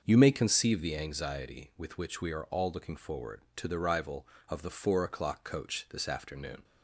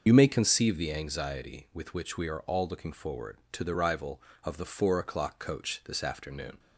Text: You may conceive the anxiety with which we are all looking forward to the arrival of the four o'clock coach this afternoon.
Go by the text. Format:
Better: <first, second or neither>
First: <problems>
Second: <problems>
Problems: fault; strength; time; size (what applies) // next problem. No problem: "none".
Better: first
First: starts louder than the rest; until 1.0 s; 6.5 dB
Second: loses the start of "You"; at 0.0 s; 60 ms // starts louder than the rest; until 1.0 s; 6 dB